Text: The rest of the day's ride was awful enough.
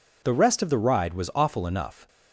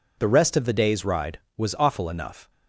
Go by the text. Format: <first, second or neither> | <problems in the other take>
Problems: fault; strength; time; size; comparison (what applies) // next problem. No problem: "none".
second | skips "day's"; at 0.7 s